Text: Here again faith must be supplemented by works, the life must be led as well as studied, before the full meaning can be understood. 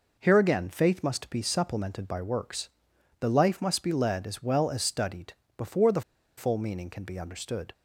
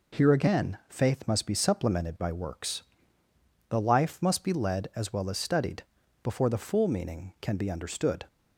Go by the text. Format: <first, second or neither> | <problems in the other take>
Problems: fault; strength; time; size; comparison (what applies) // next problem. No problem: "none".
second | pauses between "the" and "full"; slight; at 6.0 s; 0.35 s long